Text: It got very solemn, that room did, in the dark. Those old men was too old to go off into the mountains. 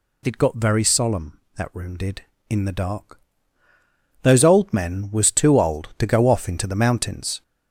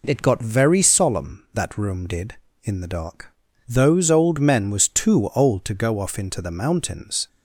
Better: second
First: gets louder; noticeable; throughout; 5.5 dB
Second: none

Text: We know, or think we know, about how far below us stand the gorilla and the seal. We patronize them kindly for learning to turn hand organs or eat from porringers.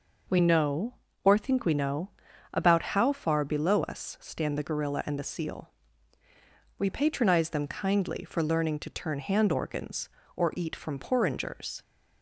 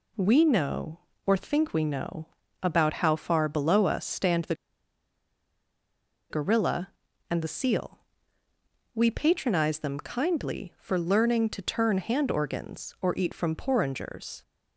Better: first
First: none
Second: pauses between "the" and "gorilla"; strong; at 4.5 s; 1.7 s long

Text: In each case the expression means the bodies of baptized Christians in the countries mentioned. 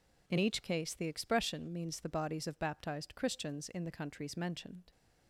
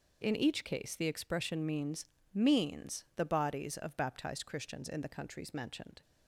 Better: first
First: none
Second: says "means" twice; at 2.3 s

